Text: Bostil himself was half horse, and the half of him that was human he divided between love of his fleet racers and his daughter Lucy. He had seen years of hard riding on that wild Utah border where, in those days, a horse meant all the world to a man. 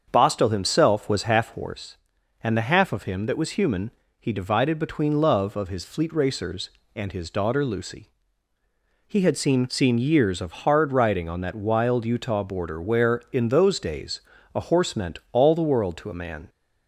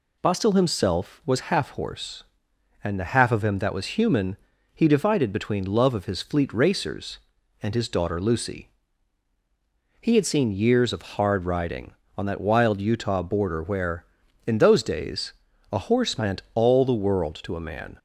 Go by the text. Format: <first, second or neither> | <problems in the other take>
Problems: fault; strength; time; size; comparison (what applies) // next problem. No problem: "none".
second | starts louder than the rest; until 1.1 s; 7 dB // pauses between "human" and "he"; slight; at 3.9 s; 0.28 s long; also in the second // says "seen" twice; at 9.6 s